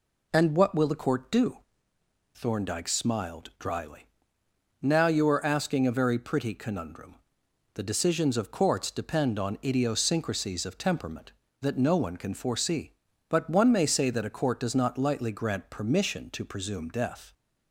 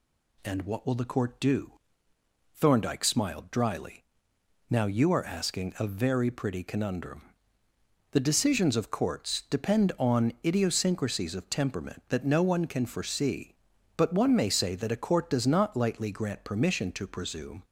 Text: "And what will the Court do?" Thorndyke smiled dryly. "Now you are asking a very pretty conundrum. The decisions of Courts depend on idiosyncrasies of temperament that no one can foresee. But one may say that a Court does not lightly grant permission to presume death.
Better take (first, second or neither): first